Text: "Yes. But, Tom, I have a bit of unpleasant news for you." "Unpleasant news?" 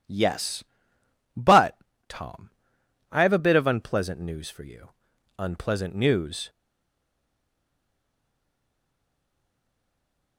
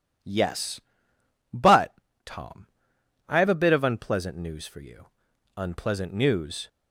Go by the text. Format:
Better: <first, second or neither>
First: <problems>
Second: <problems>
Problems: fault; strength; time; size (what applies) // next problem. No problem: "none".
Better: second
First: stays silent after the last word; strong; from 6.4 s on; 3.9 s long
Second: none